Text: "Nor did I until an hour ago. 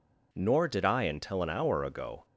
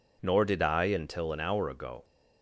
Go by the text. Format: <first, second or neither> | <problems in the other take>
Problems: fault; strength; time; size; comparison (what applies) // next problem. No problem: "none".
neither | none